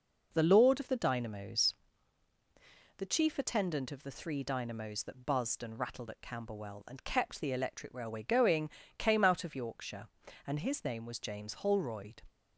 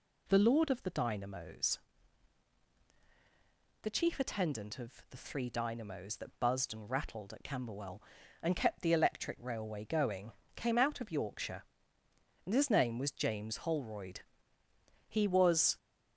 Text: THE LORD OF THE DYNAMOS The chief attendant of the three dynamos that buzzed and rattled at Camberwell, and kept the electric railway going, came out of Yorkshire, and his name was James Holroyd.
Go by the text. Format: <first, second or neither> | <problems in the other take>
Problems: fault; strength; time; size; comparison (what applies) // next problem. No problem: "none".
first | pauses between "DYNAMOS" and "The"; strong; at 1.7 s; 2.0 s long; strong in the first // pauses between "of" and "the"; slight; at 4.9 s; 0.18 s long // goes on to say "He was"; noticeable; from 15.0 s on; 0.70 s long